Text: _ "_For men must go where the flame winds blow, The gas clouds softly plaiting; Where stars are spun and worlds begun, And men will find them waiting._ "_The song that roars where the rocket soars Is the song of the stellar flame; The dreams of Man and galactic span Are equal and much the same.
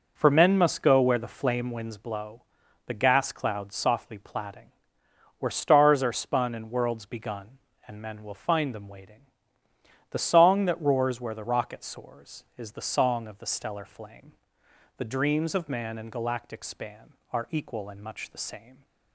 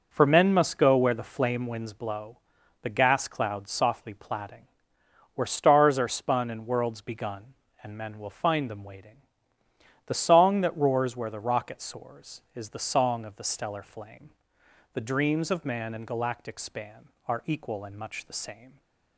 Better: neither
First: none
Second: none

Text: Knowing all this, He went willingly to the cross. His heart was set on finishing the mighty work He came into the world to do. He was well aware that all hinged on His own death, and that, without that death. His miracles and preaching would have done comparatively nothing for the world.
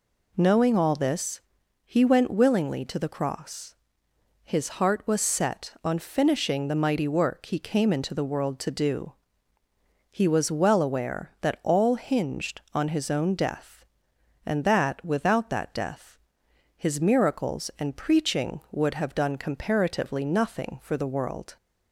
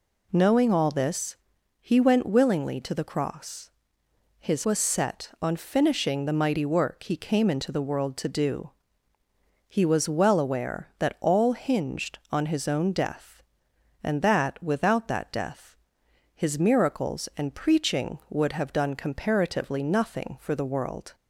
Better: first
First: none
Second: skips "heart"; at 4.6 s

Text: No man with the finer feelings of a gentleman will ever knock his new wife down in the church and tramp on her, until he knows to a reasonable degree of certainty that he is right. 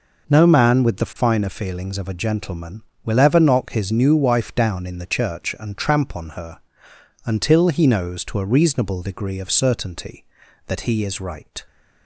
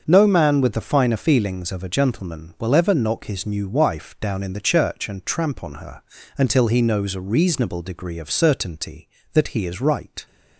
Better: first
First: none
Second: starts louder than the rest; until 1.0 s; 6.5 dB // skips "to"; at 7.1 s

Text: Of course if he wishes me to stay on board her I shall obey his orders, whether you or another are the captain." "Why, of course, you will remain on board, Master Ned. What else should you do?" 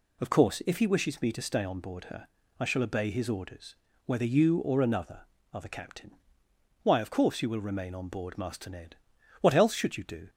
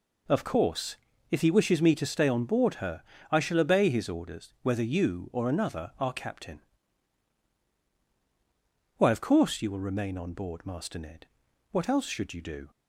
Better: first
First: pauses between "her" and "I"; slight; at 2.2 s; 0.30 s long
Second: pauses between "course" and "if"; slight; at 0.9 s; 0.34 s long // pauses between "her" and "I"; slight; at 3.0 s; 0.28 s long // skips "the"; at 6.1 s

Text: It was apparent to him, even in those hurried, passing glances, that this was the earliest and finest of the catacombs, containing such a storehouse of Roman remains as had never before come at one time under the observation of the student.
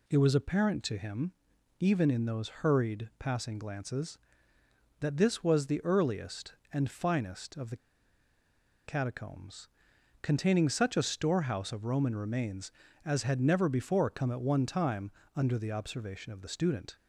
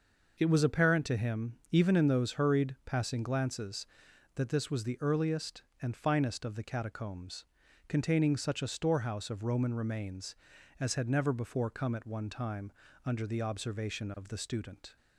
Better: second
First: pauses between "the" and "catacombs"; at 7.7 s; 1.1 s long // pauses between "time" and "under"; slight; at 15.1 s; 0.24 s long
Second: pauses between "time" and "under"; slight; at 12.6 s; 0.34 s long

